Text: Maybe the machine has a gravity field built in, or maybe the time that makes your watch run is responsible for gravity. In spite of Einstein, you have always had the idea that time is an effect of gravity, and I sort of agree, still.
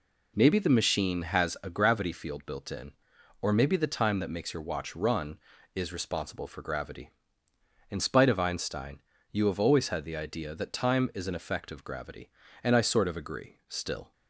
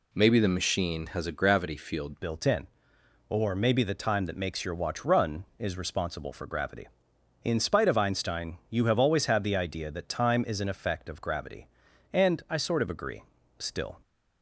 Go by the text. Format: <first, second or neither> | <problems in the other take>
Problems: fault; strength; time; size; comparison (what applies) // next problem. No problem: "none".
first | changes voice at "built"; from 2.2 s on; 11.7 s long